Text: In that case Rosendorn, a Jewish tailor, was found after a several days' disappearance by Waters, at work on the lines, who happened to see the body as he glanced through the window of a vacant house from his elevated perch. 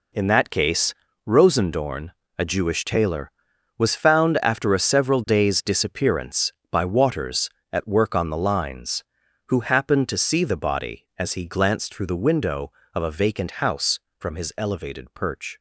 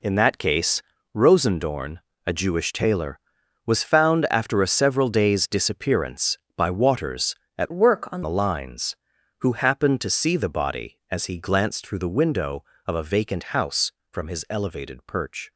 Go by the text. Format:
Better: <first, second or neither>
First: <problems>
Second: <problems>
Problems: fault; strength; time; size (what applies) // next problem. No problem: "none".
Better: first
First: pauses between "case" and "Rosendorn"; slight; at 0.9 s; 0.34 s long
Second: pauses between "case" and "Rosendorn"; slight; at 0.8 s; 0.34 s long // changes voice from "work" to "on"; from 7.7 to 8.2 s; 0.5 s long